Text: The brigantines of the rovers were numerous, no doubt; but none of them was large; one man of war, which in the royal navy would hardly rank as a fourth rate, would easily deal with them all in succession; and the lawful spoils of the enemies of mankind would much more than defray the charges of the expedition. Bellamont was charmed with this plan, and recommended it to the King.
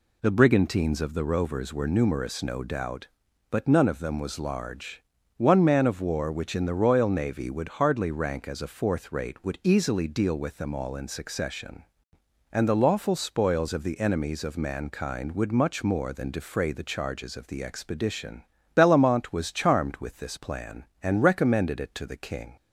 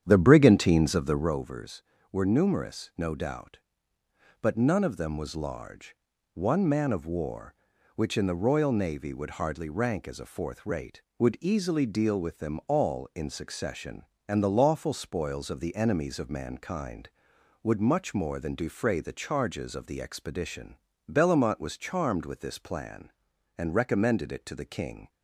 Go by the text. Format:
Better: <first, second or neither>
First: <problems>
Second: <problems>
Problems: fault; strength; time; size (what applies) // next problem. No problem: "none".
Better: first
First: none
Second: starts louder than the rest; strong; until 1.4 s; 9 dB